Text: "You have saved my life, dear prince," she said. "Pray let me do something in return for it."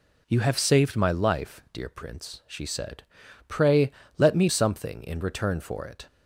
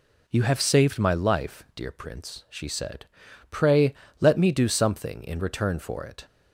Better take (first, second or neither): second